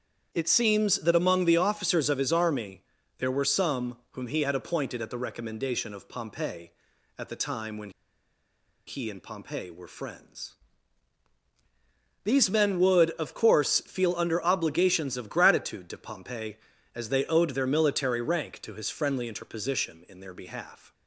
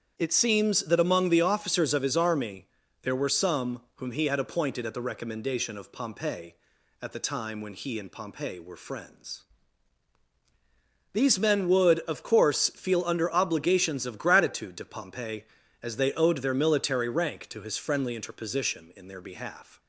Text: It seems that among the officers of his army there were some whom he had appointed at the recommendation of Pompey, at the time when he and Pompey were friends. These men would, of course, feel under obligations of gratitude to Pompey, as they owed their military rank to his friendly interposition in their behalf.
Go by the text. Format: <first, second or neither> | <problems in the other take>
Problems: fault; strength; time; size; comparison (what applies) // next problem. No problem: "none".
second | starts louder than the rest; strong; until 1.3 s; 8.5 dB; strong in the second // pauses between "army" and "there"; at 2.7 s; 0.38 s long; also in the second // pauses between "when" and "he"; noticeable; at 7.8 s; 0.97 s long